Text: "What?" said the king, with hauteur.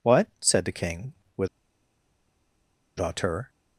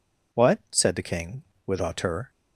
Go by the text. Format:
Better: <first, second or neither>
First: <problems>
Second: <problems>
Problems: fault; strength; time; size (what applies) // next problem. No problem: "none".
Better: second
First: pauses between "with" and "hauteur"; strong; at 1.4 s; 1.5 s long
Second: none